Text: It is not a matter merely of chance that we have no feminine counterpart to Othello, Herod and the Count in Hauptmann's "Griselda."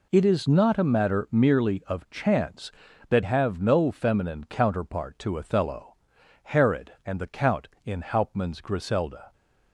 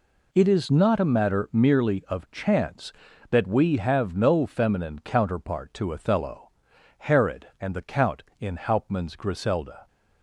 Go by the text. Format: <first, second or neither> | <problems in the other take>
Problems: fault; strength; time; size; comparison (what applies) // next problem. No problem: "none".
second | skips "we"; at 3.2 s